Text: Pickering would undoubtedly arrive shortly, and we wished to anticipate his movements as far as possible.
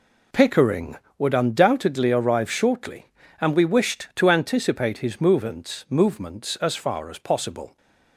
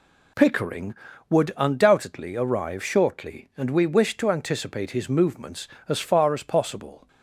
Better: second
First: says "movements" twice; at 5.8 s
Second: none

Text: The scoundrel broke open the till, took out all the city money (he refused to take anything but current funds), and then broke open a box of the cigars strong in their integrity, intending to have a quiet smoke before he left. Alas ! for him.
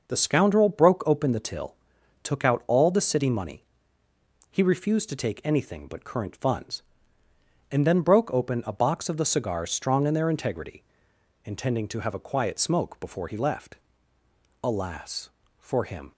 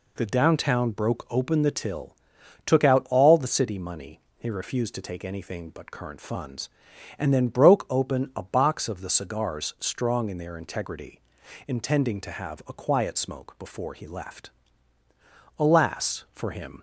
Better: first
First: none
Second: says "downtown" for "scoundrel"; at 0.2 s

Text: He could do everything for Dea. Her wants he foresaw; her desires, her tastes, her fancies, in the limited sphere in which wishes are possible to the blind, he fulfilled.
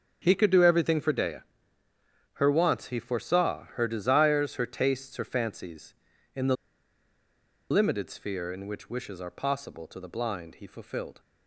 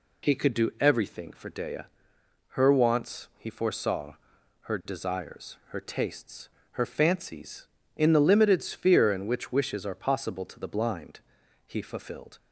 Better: second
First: starts louder than the rest; strong; until 1.2 s; 7.5 dB // pauses between "the" and "limited"; at 6.5 s; 1.1 s long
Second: none

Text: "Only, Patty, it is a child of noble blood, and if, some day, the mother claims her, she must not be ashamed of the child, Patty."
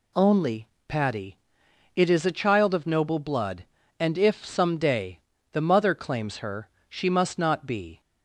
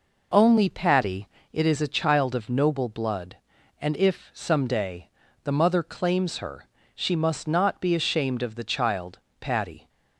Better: second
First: stops before "ashamed of the child Patty"; at 7.9 s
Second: none

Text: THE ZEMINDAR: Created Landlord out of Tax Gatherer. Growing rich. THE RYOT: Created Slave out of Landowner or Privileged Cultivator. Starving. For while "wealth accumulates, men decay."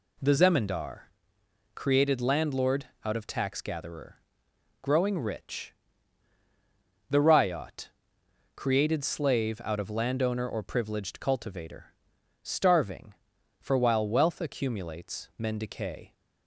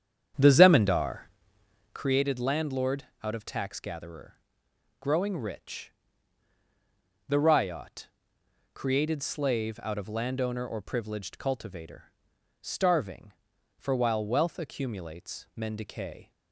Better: first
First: pauses between "Landlord" and "out"; slight; at 2.8 s; 0.18 s long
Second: starts louder than the rest; strong; until 2.1 s; 8.5 dB // pauses between "Landlord" and "out"; slight; at 3.0 s; 0.18 s long

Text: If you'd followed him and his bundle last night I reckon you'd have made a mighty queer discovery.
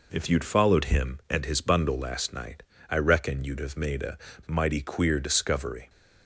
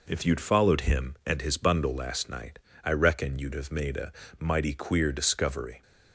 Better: neither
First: pauses between "night" and "I"; slight; at 2.6 s; 0.26 s long // pauses between "a" and "mighty"; slight; at 4.1 s; 0.28 s long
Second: pauses between "night" and "I"; slight; at 2.5 s; 0.24 s long // pauses between "a" and "mighty"; slight; at 4.1 s; 0.26 s long

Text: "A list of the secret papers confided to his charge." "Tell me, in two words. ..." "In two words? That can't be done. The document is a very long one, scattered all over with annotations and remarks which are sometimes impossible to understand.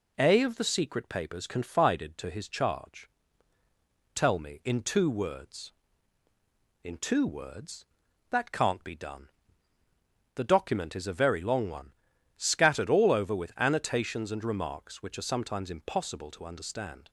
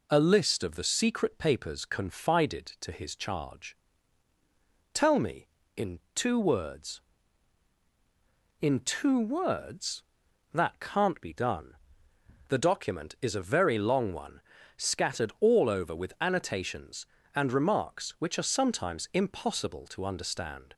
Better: second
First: skips "list"; at 0.4 s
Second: none

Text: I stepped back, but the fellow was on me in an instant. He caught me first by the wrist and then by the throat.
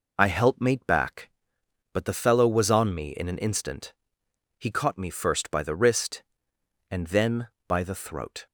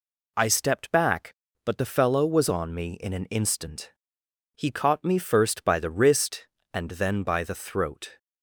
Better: second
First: says "helpmate" for "stepped"; at 0.2 s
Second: none

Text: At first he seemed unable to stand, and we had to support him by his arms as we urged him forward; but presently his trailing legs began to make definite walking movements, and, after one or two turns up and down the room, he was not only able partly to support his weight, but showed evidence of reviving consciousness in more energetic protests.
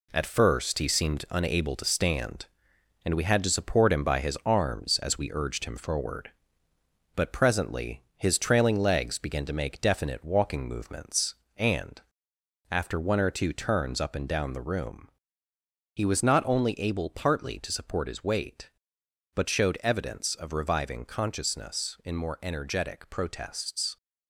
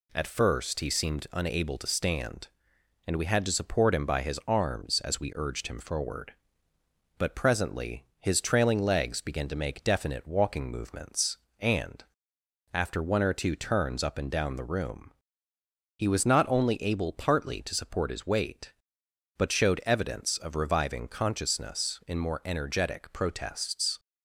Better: second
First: gets quieter; throughout; 7 dB // pauses between "presently" and "his"; slight; at 8.0 s; 0.16 s long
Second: pauses between "presently" and "his"; slight; at 8.0 s; 0.16 s long

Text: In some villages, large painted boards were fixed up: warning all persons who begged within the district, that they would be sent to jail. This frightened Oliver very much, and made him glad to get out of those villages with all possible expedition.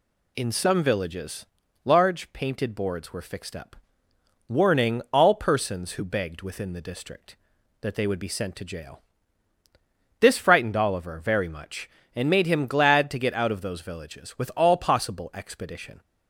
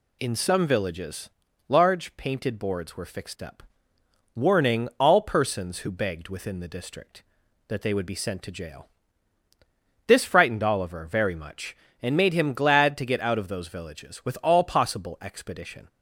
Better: neither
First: none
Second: none

